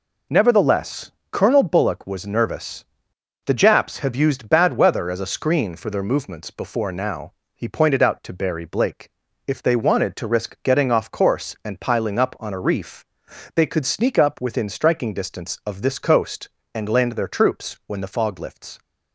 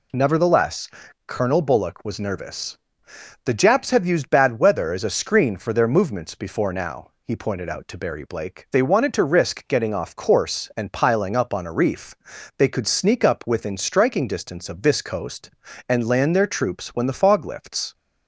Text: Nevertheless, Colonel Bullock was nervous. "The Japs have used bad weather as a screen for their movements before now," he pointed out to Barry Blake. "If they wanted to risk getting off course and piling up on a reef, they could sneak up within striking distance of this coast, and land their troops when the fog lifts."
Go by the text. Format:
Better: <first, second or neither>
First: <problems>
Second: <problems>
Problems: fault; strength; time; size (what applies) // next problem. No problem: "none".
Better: first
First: none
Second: skips "If"; at 8.6 s